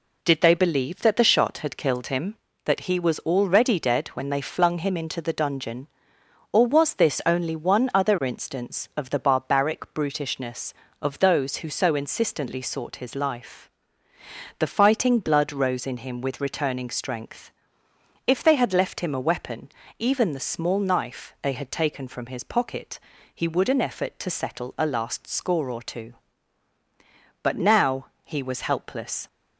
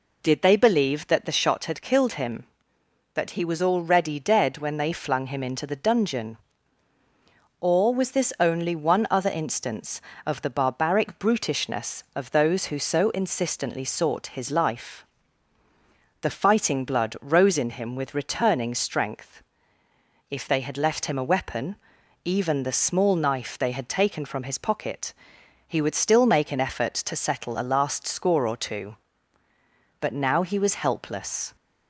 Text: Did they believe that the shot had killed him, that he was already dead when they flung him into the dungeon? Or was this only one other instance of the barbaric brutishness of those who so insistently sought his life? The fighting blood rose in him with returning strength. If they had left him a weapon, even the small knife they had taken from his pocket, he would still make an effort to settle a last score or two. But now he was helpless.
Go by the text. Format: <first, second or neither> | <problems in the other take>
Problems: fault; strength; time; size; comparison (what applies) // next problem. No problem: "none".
second | skips "still make"; at 23.6 s // pauses between "now" and "he"; slight; at 28.0 s; 0.18 s long